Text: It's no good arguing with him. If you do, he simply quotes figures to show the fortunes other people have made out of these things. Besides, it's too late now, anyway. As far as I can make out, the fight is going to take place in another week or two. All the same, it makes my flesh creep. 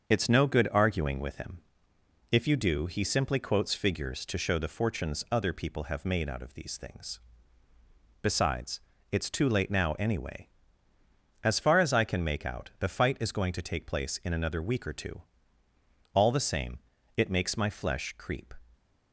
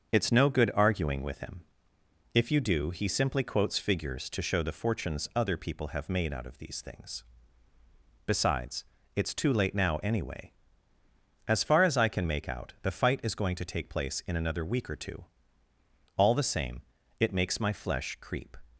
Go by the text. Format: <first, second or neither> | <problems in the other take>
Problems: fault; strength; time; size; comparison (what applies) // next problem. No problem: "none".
neither | starts louder than the rest; the same in both